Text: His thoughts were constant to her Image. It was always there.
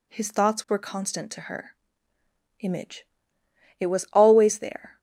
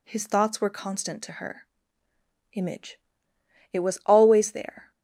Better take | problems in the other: neither | pauses between "her" and "Image"; noticeable; the same in both

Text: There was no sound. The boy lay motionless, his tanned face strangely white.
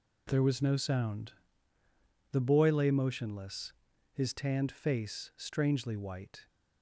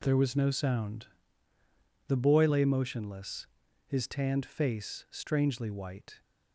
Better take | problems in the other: neither | none

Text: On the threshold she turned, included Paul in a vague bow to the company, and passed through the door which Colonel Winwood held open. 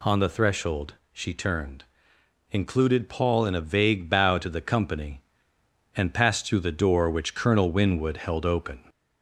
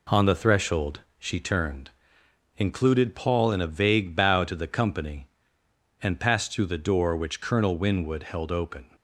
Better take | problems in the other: second | gets louder; slight; throughout; 2.5 dB // pauses between "threshold" and "she"; slight; at 0.9 s; 0.16 s long; slight in the second

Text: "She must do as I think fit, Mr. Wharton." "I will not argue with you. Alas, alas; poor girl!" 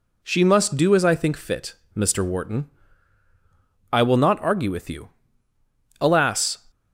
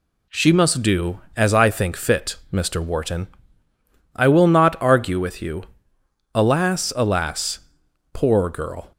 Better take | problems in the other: second | stops before "alas poor girl"; at 6.7 s

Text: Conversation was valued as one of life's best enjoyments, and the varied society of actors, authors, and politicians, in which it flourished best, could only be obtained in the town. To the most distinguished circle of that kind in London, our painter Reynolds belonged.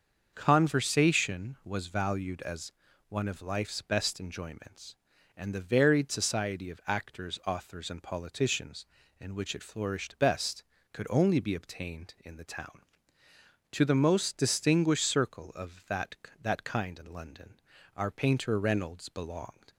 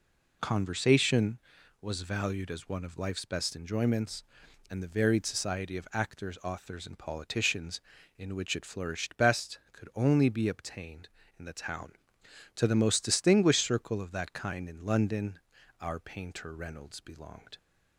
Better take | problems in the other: second | starts louder than the rest; until 1.3 s; 6.5 dB // pauses between "as" and "one"; at 2.7 s; 0.38 s long // says "that" twice; at 16.4 s

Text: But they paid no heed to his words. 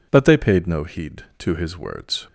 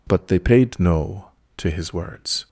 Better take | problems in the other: first | skips "heed"; at 1.4 s

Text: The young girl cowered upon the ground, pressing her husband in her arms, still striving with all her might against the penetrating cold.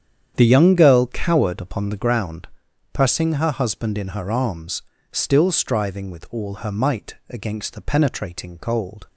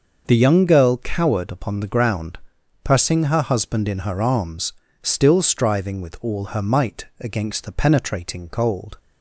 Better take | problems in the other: second | starts louder than the rest; strong; until 2.1 s; 8.5 dB // pauses between "might" and "against"; slight; at 7.1 s; 0.16 s long; slight in the second

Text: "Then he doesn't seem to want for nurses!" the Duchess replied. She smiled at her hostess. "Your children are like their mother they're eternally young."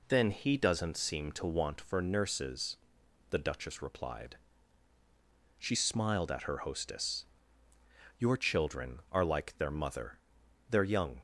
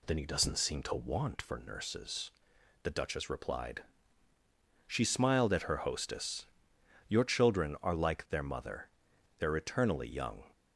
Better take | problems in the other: second | pauses between "mother" and "they're"; noticeable; at 10.1 s; 0.54 s long; noticeable in the second // skips "eternally"; at 10.8 s

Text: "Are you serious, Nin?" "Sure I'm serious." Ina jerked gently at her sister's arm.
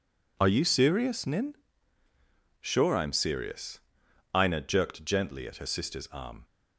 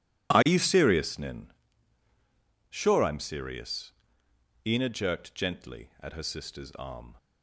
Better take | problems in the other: neither | none

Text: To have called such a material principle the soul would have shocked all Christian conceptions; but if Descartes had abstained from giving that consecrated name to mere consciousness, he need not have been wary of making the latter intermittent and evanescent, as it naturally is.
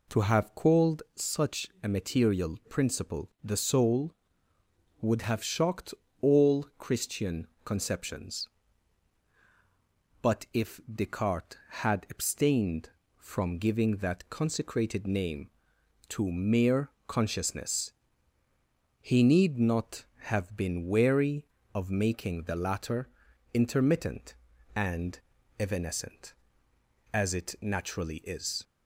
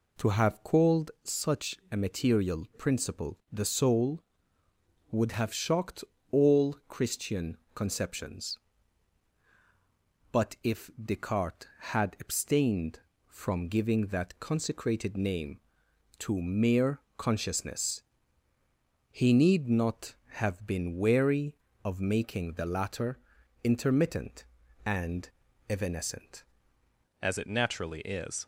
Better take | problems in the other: first | pauses between "such" and "a"; slight; at 1.7 s; 0.16 s long; slight in the first // pauses between "shocked" and "all"; slight; at 6.0 s; 0.28 s long; slight in the first // pauses between "Christian" and "conceptions"; slight; at 7.5 s; 0.20 s long; slight in the first // pauses between "mere" and "consciousness"; slight; at 16.9 s; 0.18 s long; slight in the first // pauses between "latter" and "intermittent"; at 23.1 s; 0.44 s long; also in the first // pauses between "and" and "evanescent"; at 25.2 s; 0.40 s long; also in the first // changes voice at "as"; from 27.2 s on; 1.2 s long

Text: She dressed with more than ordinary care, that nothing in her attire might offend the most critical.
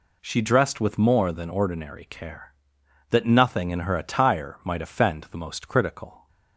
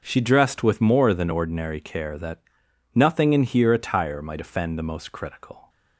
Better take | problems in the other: first | starts louder than the rest; until 1.0 s; 6 dB // pauses between "that" and "nothing"; noticeable; at 2.4 s; 0.52 s long // says "here" for "her"; at 3.4 s

